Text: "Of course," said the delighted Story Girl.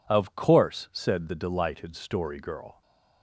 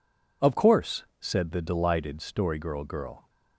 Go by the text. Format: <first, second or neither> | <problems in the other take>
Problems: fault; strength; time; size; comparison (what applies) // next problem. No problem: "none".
first | says "Girl" twice; at 2.8 s